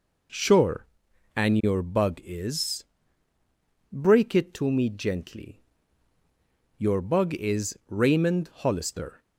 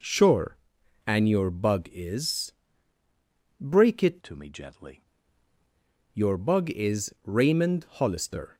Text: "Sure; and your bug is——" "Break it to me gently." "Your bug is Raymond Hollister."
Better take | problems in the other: first | changes voice from "to" to "gently"; from 4.2 to 5.0 s; 0.8 s long

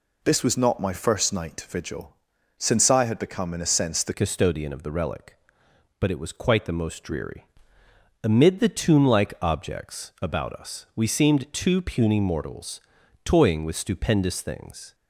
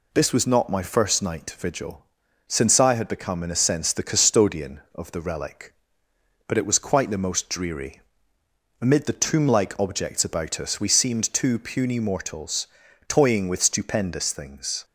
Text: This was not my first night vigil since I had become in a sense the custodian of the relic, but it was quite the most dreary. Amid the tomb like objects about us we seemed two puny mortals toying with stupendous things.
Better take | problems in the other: second | pauses between "vigil" and "since"; at 2.1 s; 0.40 s long; also in the second // changes voice at "custodian"; from 4.1 s on; 10.8 s long // pauses between "mortals" and "toying"; noticeable; at 12.7 s; 0.46 s long; also in the second

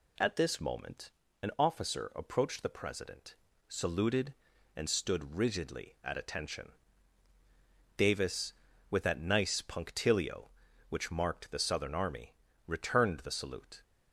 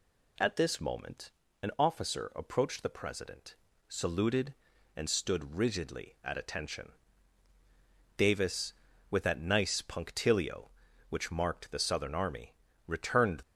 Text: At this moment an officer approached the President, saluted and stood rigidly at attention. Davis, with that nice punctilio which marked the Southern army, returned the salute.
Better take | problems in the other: first | pauses between "moment" and "an"; slight; at 1.3 s; 0.32 s long; slight in the first // stops before "the salute"; at 13.4 s

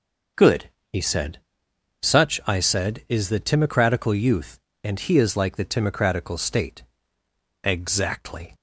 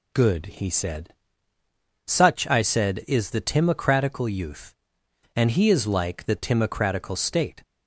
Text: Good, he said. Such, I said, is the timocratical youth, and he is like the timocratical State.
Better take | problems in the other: second | starts louder than the rest; until 2.2 s; 6.5 dB // goes on to say "Exactly"; noticeable; from 7.6 s on; 0.92 s long

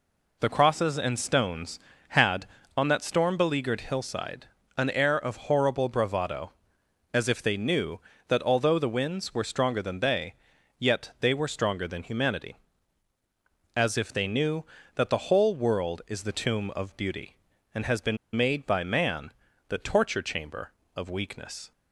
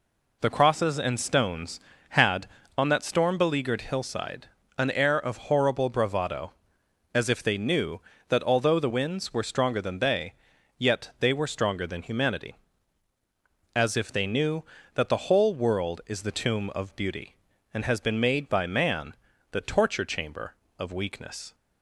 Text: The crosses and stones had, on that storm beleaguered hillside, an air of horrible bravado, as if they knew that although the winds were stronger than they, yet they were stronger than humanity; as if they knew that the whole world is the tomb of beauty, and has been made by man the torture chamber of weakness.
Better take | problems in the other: second | pauses between "been" and "made"; slight; at 18.1 s; 0.18 s long // pauses between "man" and "the"; at 19.3 s; 0.38 s long; also in the second

